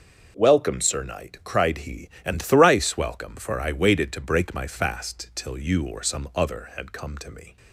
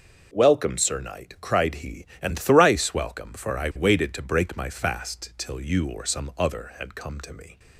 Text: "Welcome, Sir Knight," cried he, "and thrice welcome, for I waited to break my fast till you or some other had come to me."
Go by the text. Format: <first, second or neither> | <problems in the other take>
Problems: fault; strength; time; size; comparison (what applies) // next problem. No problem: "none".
neither | starts louder than the rest; noticeable; the same in both